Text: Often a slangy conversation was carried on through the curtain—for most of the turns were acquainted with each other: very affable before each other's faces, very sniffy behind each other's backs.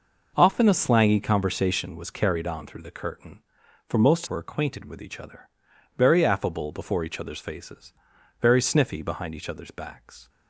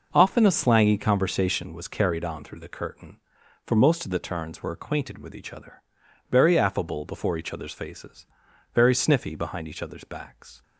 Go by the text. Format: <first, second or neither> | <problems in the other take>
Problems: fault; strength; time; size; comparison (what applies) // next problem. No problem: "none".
second | skips "of the turns"; at 4.2 s